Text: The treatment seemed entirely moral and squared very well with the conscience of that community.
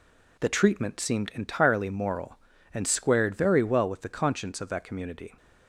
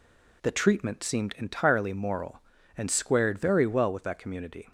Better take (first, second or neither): first